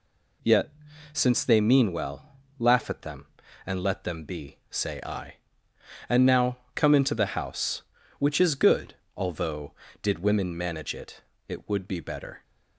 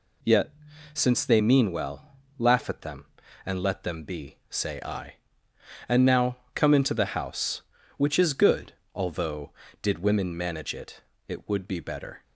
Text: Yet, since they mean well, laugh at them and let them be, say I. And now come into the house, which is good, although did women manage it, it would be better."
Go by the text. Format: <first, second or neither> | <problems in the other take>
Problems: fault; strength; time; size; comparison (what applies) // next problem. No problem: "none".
neither | pauses between "now" and "come"; slight; the same in both